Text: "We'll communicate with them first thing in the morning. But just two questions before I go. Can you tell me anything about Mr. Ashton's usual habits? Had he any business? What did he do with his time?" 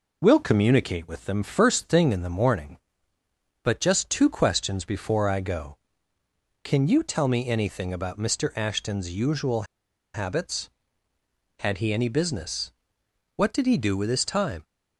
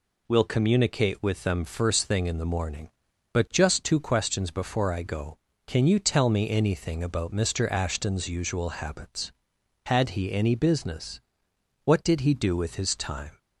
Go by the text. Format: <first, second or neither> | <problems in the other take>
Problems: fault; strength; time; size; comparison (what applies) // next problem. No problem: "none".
second | pauses between "usual" and "habits"; noticeable; at 9.6 s; 0.50 s long